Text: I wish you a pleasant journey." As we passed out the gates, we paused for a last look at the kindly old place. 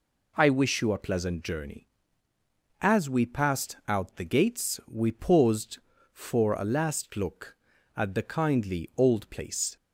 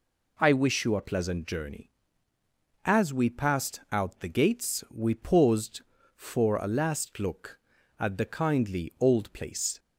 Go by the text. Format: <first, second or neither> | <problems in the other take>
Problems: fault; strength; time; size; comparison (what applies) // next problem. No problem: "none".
neither | none